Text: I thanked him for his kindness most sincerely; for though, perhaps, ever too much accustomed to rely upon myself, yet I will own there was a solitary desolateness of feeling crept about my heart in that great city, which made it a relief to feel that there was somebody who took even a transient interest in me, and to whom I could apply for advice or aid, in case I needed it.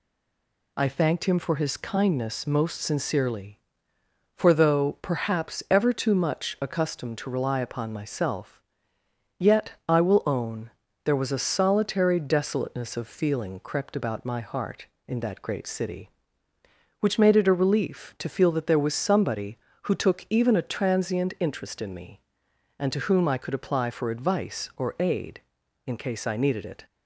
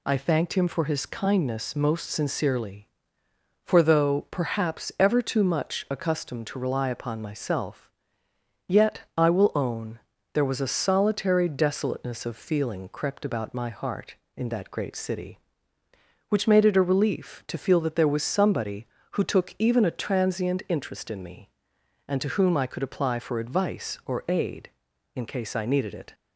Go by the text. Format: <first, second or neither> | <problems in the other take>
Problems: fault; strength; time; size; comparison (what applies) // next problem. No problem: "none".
second | stays silent before the first word; slight; until 0.7 s; 0.7 s long // pauses between "own" and "there"; slight; at 10.7 s; 0.34 s long; slight in the second